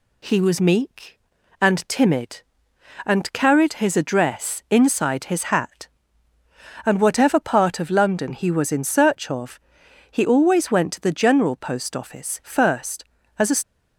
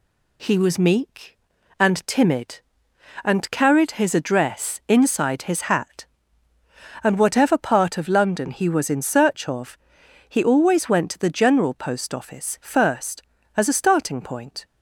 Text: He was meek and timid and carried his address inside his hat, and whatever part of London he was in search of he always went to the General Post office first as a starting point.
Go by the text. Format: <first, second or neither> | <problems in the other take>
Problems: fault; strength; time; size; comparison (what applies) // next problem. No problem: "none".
second | pauses between "of" and "he"; noticeable; at 9.5 s; 0.50 s long; noticeable in the second // stops before "starting point"; at 13.6 s